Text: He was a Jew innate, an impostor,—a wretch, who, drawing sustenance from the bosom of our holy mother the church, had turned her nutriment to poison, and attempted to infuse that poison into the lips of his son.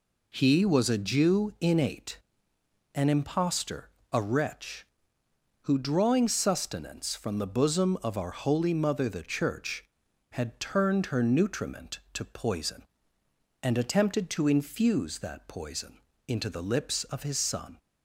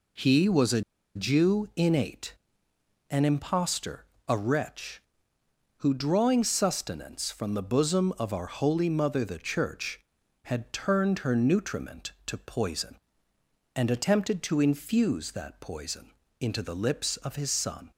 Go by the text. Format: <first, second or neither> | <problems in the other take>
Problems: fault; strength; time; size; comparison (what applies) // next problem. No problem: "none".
first | pauses between "a" and "Jew"; slight; at 0.8 s; 0.34 s long // pauses between "poison" and "into"; slight; at 16.1 s; 0.28 s long; slight in the first